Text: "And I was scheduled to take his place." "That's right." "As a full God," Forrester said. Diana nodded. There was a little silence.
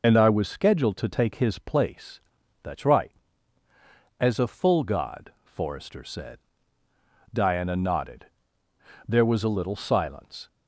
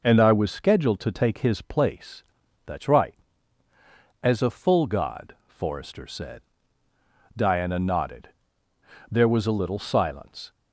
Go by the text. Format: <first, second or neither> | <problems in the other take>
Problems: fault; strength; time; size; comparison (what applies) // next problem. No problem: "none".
second | loses the start of "And"; at 0.0 s; 30 ms